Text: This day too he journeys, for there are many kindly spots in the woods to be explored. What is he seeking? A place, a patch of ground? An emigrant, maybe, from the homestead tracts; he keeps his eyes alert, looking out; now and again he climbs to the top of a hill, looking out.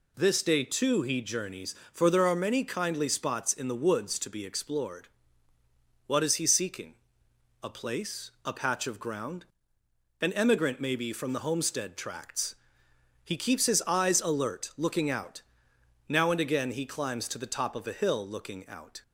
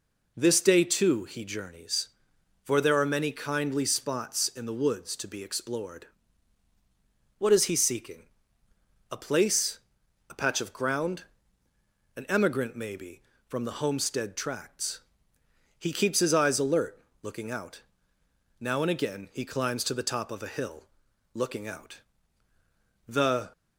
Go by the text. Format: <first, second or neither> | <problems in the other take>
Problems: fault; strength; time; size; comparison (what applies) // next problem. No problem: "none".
first | goes on to say "The"; slight; from 23.0 s on; 0.46 s long